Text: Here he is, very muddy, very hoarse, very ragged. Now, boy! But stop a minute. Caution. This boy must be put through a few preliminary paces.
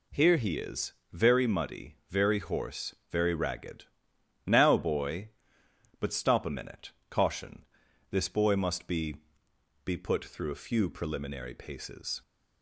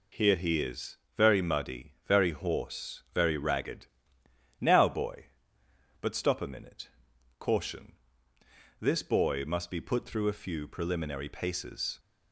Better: second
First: says "be" twice; at 9.8 s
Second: none

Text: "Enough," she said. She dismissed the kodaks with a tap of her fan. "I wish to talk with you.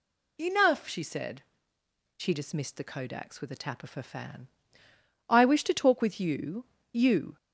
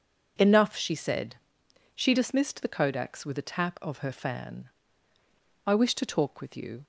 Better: second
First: says "you" twice; at 6.9 s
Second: none

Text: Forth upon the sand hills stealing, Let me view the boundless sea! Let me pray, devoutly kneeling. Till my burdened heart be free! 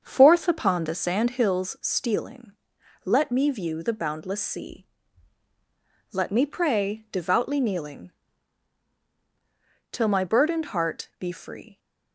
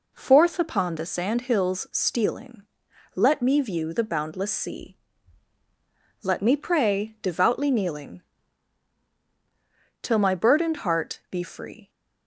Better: second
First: starts louder than the rest; until 1.6 s; 7 dB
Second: none

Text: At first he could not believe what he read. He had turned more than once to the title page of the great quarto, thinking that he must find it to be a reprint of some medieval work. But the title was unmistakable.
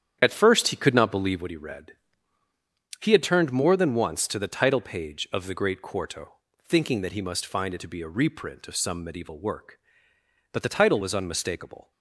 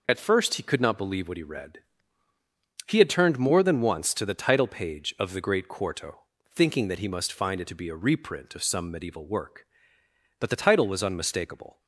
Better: second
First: starts louder than the rest; strong; until 1.5 s; 9.5 dB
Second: none

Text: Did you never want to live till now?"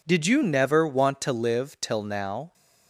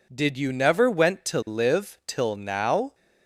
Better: first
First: none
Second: says "went" for "want"; at 0.8 s

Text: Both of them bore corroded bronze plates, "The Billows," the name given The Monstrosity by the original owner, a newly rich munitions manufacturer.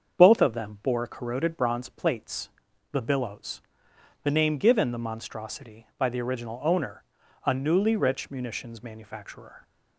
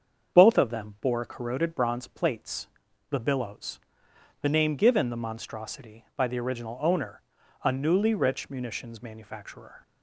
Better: neither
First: starts louder than the rest; until 1.2 s; 7 dB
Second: starts louder than the rest; until 1.4 s; 7 dB

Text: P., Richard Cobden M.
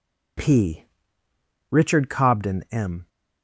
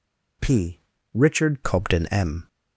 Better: first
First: none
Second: changes voice at "Cobden"; from 1.6 s on; 0.8 s long

